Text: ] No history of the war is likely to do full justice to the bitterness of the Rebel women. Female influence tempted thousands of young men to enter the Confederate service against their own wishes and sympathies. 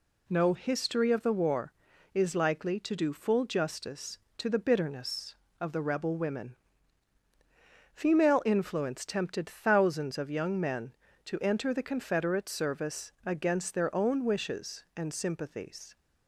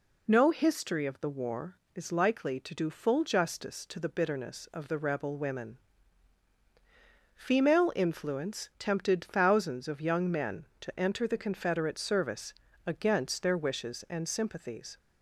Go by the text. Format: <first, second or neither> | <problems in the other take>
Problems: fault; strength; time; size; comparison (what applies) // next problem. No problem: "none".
first | pauses between "service" and "against"; slight; at 12.5 s; 0.34 s long // skips "own"; at 13.5 s